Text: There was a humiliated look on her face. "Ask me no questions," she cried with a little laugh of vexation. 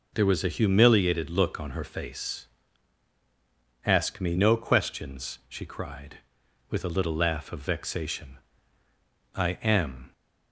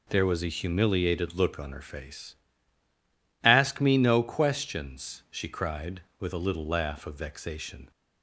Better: second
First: goes on to say "I am"; noticeable; from 9.3 s on; 0.78 s long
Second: none

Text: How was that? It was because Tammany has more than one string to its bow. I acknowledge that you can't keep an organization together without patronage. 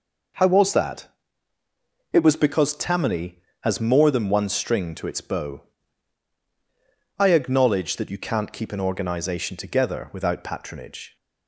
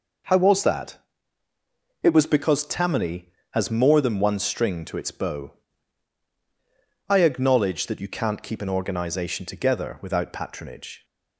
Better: neither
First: none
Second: none

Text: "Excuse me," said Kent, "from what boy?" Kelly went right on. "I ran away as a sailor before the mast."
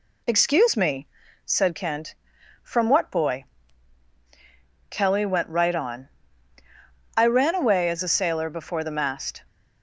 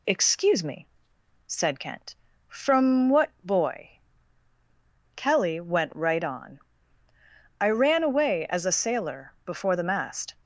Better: neither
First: none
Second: none

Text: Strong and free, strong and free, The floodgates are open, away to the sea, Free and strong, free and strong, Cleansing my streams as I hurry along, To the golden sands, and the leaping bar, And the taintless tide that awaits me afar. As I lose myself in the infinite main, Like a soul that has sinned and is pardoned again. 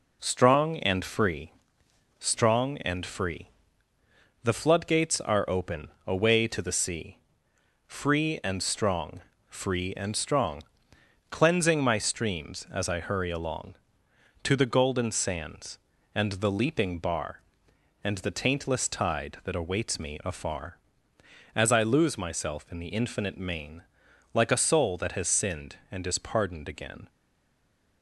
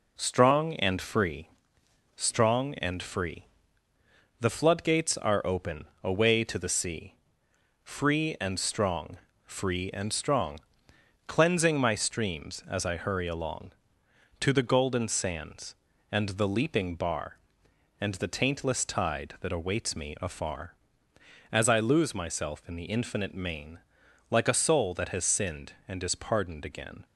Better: second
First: stays silent after the last word; slight; from 27.0 s on; 1.0 s long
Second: none

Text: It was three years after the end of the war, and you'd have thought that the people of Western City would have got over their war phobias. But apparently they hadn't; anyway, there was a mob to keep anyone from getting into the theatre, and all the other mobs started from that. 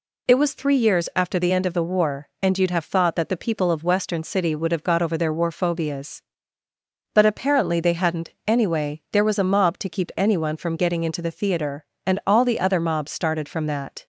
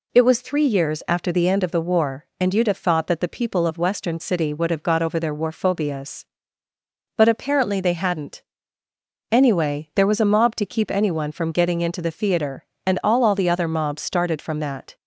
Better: first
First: none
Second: says "all" twice; at 13.2 s

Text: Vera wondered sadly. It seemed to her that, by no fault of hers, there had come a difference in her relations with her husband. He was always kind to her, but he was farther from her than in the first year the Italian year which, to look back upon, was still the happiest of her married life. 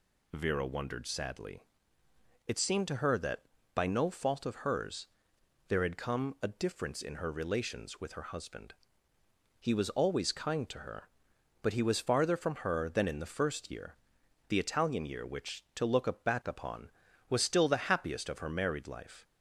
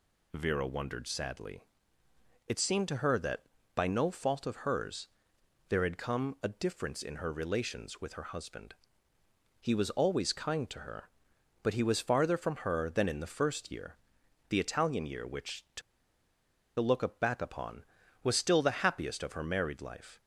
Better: first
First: pauses between "year" and "the"; noticeable; at 13.9 s; 0.52 s long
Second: pauses between "year" and "the"; noticeable; at 13.9 s; 0.52 s long // pauses between "to" and "look"; noticeable; at 15.8 s; 0.98 s long

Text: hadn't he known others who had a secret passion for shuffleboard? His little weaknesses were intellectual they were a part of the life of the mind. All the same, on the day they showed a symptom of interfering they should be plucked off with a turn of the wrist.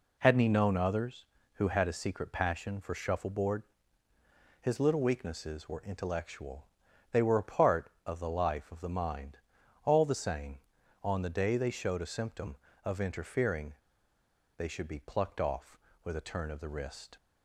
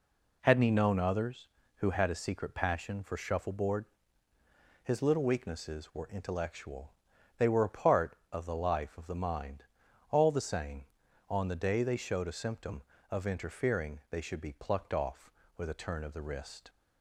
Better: second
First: pauses between "intellectual" and "they"; noticeable; at 6.6 s; 0.48 s long // pauses between "interfering" and "they"; noticeable; at 13.7 s; 0.87 s long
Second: pauses between "intellectual" and "they"; noticeable; at 6.9 s; 0.48 s long

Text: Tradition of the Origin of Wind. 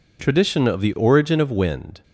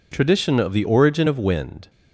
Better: neither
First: none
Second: none

